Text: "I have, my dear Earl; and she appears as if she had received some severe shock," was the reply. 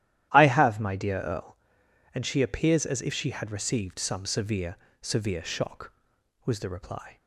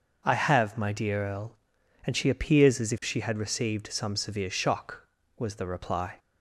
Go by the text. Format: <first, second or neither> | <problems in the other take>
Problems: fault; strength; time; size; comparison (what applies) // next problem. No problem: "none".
second | starts louder than the rest; strong; until 1.3 s; 12.5 dB; also in the second // says "severe" twice; at 5.0 s